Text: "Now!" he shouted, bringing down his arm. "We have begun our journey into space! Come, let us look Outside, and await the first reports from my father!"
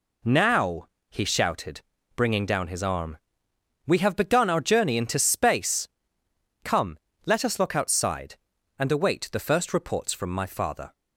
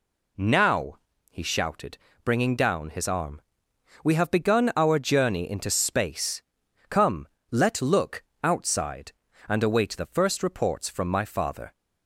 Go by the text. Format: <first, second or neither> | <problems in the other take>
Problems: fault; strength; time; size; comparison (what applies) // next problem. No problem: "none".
first | skips "us"; at 7.8 s // pauses between "look" and "Outside"; slight; at 8.2 s; 0.20 s long